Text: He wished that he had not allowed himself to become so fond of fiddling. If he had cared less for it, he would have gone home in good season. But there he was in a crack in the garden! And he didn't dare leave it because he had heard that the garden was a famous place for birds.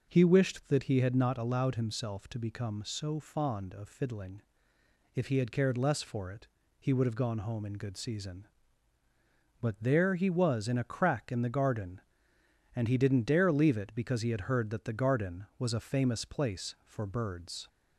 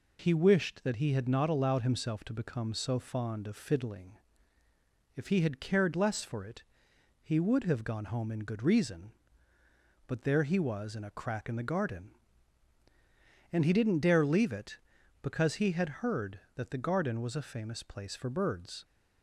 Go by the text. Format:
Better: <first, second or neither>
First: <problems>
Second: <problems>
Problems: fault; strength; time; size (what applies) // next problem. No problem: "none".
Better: first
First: none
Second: says "reason" for "season"; at 8.6 s